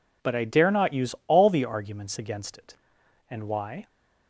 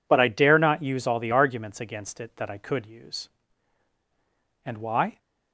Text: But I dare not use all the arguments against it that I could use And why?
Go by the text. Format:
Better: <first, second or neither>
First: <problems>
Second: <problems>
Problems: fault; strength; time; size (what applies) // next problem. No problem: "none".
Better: second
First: skips "that I could use"; at 3.0 s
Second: none